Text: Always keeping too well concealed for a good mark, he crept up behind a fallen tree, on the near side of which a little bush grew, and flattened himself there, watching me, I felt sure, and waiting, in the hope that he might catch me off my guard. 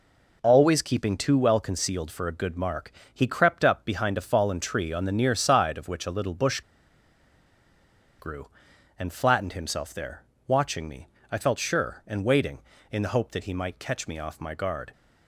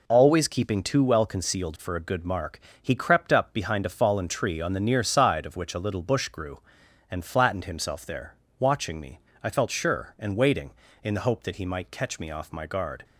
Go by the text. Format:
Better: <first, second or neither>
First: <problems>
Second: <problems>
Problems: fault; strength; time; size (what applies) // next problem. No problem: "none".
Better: second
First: pauses between "bush" and "grew"; strong; at 6.6 s; 1.5 s long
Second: none